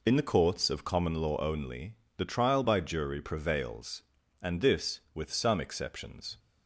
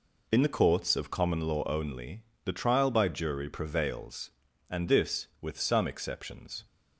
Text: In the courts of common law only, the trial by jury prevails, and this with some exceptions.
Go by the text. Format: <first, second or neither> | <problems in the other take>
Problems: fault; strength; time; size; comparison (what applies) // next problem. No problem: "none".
neither | none